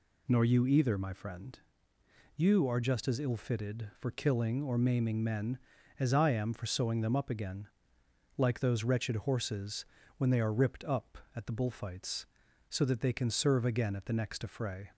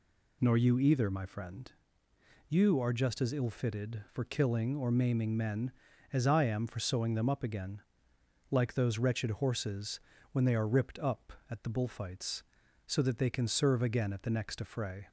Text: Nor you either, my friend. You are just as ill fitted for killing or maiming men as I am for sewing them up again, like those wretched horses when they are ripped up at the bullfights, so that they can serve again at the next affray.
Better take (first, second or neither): neither